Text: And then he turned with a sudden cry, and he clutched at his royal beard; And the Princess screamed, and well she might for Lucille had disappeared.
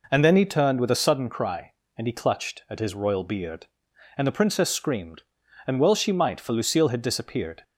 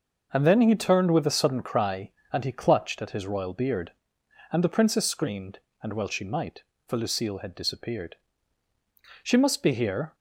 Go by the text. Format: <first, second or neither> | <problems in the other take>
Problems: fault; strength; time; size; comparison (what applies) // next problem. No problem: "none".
first | starts louder than the rest; until 1.3 s; 6.5 dB // goes on to say "She must be here"; noticeable; from 8.9 s on; 1.1 s long